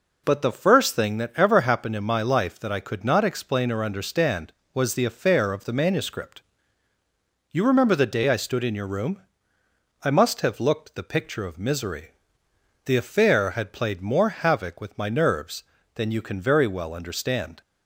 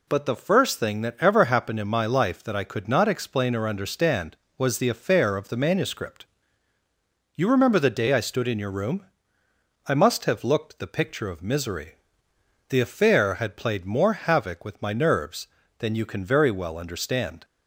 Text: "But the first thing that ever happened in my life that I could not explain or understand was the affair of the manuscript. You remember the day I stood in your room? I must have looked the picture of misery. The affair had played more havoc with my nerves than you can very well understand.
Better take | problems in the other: second | starts louder than the rest; noticeable; until 1.2 s; 4.5 dB

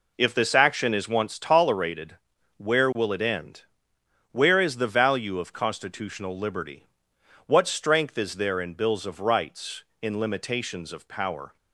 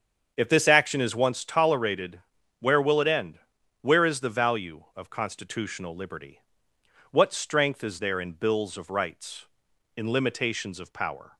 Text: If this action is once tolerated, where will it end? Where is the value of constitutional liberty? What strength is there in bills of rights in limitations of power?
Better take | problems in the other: first | starts louder than the rest; strong; until 1.4 s; 7 dB

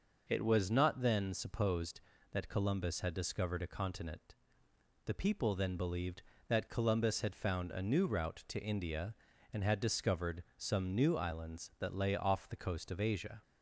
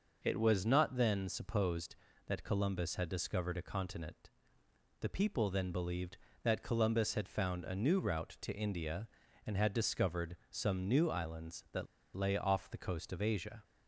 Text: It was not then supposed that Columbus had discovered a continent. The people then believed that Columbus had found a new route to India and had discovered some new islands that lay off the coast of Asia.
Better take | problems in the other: first | pauses between "that" and "lay"; slight; at 11.8 s; 0.30 s long

